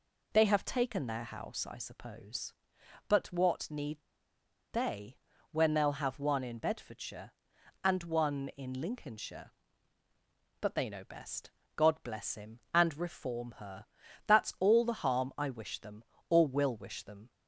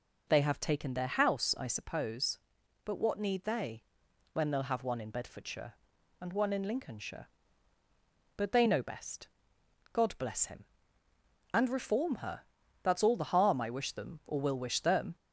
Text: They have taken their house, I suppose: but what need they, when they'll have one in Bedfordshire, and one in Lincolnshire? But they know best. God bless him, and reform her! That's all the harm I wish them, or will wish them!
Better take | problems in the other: second | pauses between "need" and "they"; noticeable; at 3.9 s; 0.73 s long

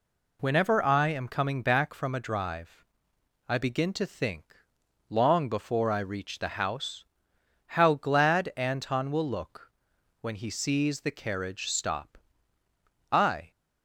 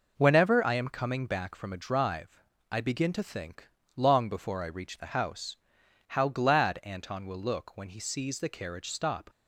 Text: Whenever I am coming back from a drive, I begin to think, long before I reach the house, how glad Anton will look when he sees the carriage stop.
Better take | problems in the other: second | pauses between "look" and "when"; noticeable; at 9.7 s; 0.52 s long // goes on to say "I"; slight; from 13.1 s on; 0.38 s long

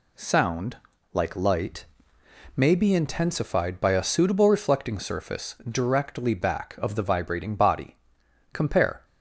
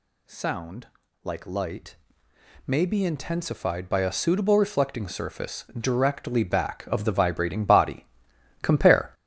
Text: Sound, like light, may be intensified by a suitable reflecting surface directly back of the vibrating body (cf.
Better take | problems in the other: first | gets louder; throughout; 7 dB

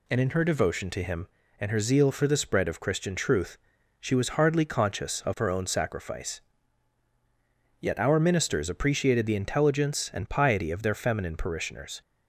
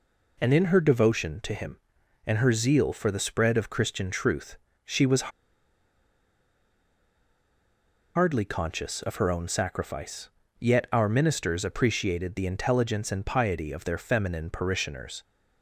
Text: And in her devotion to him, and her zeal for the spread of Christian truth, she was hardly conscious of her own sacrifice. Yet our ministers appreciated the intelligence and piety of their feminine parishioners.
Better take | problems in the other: first | pauses between "was" and "hardly"; strong; at 5.3 s; 2.8 s long

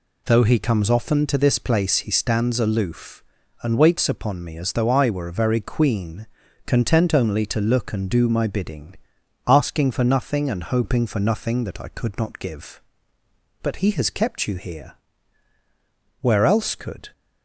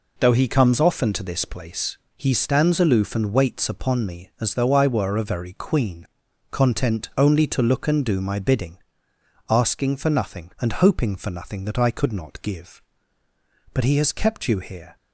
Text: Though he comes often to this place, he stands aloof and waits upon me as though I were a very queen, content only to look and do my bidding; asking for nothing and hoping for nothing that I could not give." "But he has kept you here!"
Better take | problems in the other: second | goes on to say "Where else could"; noticeable; from 16.1 s on; 0.92 s long

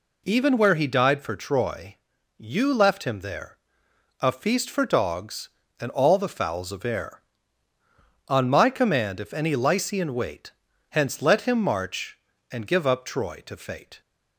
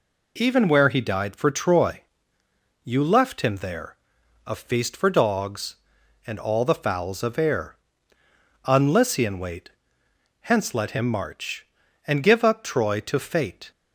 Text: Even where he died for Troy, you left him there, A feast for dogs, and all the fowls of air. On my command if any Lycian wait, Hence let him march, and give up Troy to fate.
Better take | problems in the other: first | skips "my command if any"; at 8.9 s

